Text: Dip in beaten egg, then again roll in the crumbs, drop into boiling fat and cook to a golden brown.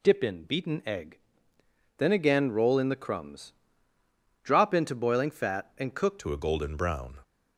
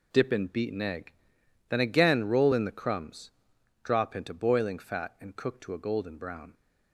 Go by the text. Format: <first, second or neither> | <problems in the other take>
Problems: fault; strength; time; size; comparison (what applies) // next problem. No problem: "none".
second | changes voice at "to"; from 6.1 s on; 1.0 s long